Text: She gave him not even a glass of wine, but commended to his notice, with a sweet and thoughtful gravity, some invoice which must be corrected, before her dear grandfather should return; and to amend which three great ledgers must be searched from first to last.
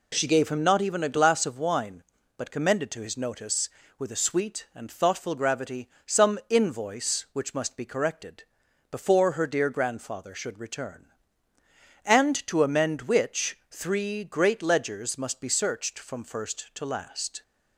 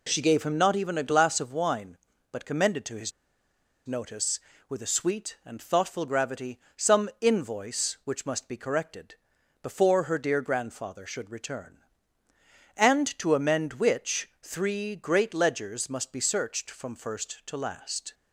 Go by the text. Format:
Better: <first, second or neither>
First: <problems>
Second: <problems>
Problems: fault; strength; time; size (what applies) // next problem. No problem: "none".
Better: first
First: none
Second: pauses between "his" and "notice"; noticeable; at 3.1 s; 0.74 s long